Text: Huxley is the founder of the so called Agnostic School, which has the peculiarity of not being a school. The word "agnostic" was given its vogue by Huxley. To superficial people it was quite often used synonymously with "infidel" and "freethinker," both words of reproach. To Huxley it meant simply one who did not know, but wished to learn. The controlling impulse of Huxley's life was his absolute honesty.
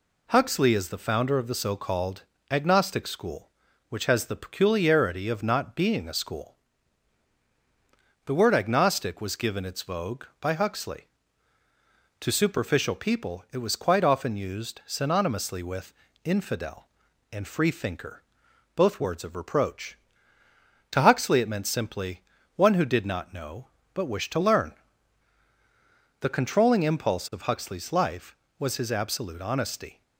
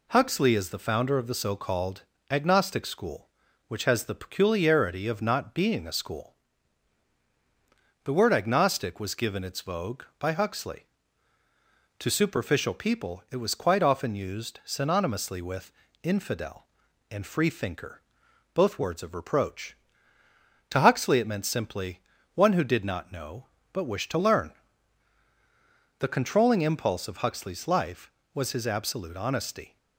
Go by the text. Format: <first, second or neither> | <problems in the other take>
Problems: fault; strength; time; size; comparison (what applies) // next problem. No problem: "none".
neither | pauses between "called" and "Agnostic"; slight; the same in both // pauses between "with" and "infidel"; slight; the same in both // pauses between "simply" and "one"; slight; the same in both